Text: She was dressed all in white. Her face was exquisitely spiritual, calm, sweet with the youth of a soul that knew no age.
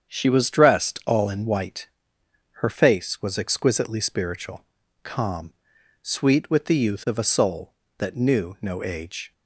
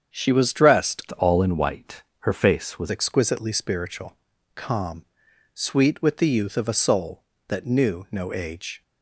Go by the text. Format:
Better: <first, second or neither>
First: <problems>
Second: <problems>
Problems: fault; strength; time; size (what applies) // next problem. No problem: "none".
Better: first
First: starts louder than the rest; strong; until 1.1 s; 8 dB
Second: starts louder than the rest; strong; until 1.3 s; 8 dB // changes voice from "all" to "was"; from 1.1 to 2.8 s; 1.7 s long